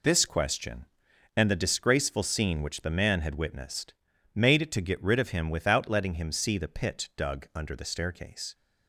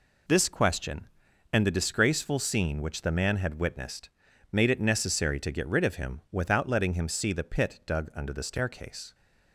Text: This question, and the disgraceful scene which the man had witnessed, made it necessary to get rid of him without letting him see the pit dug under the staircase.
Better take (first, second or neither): second